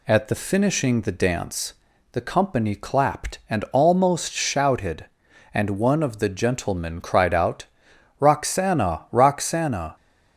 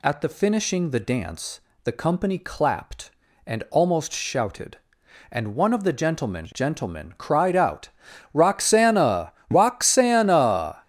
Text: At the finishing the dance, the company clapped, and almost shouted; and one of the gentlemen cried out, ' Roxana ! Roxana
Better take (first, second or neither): first